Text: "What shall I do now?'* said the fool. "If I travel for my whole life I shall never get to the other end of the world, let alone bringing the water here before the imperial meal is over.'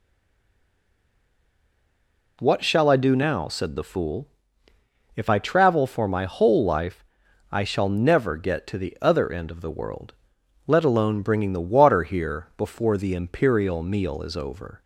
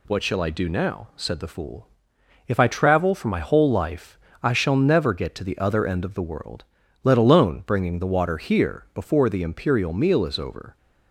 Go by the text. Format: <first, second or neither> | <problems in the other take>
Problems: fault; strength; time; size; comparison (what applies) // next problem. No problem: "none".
second | stays silent before the first word; until 2.4 s; 2.4 s long // pauses between "life" and "I"; noticeable; at 7.0 s; 0.48 s long; slight in the second